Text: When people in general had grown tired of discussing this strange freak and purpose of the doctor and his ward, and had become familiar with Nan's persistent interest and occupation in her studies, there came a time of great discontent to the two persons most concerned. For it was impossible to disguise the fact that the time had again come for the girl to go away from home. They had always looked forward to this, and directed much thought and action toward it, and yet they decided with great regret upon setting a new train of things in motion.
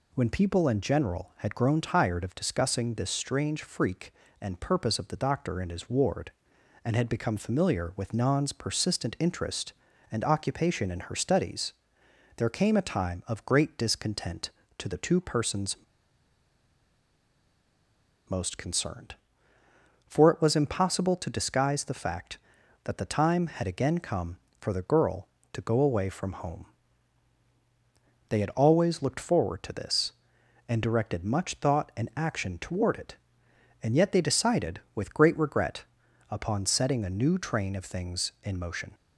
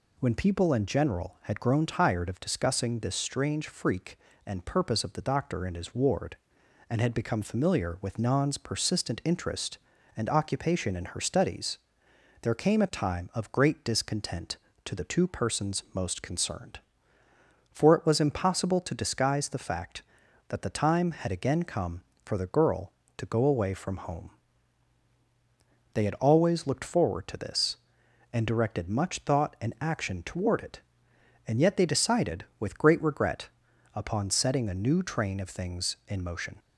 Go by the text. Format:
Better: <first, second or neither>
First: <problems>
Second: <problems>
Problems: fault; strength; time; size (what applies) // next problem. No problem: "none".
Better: second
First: pauses between "persons" and "most"; strong; at 15.7 s; 2.5 s long // pauses between "regret" and "upon"; noticeable; at 35.8 s; 0.46 s long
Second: pauses between "regret" and "upon"; noticeable; at 33.4 s; 0.46 s long